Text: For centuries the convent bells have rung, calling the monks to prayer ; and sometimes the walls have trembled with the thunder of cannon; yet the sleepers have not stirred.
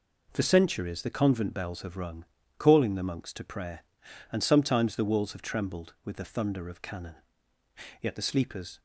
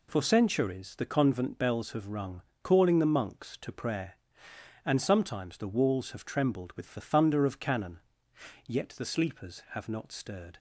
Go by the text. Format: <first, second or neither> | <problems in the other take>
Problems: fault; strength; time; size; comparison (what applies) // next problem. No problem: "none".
second | stops before "have not stirred"; at 8.7 s